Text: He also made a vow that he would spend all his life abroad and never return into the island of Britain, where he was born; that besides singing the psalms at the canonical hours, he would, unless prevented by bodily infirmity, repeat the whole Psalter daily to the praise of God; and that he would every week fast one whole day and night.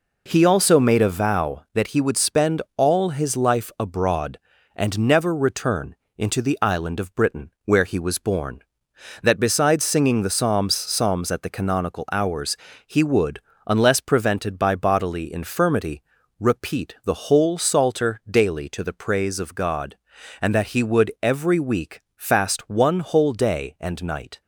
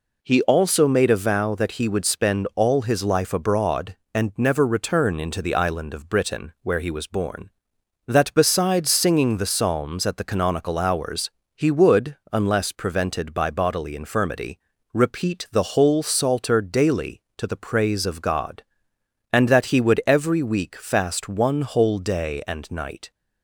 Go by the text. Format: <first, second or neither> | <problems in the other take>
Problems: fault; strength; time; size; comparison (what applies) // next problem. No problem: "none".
second | pauses between "return" and "into"; slight; at 5.9 s; 0.22 s long // says "psalms" twice; at 10.7 s // pauses between "week" and "fast"; slight; at 22.0 s; 0.16 s long